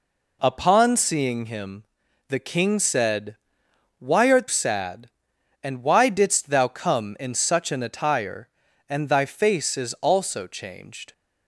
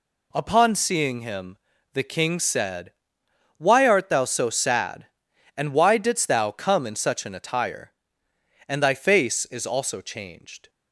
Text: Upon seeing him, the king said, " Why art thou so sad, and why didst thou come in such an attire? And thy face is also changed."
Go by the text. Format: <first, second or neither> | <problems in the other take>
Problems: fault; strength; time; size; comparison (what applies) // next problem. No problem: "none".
second | skips "thou so"; at 4.4 s